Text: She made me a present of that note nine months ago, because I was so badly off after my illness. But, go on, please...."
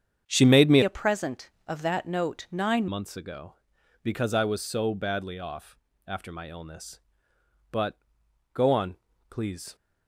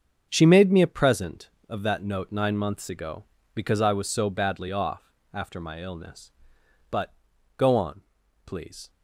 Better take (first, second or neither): second